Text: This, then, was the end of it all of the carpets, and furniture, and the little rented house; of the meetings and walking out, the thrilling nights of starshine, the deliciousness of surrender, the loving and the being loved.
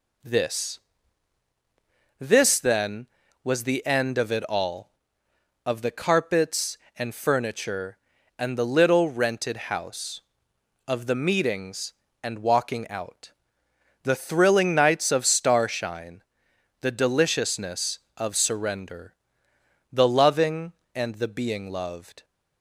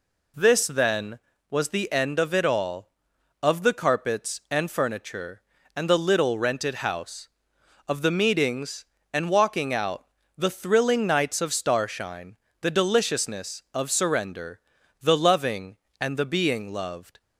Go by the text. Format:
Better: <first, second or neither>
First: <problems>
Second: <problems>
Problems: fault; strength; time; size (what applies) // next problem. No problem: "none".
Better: second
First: says "This" twice; at 2.2 s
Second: none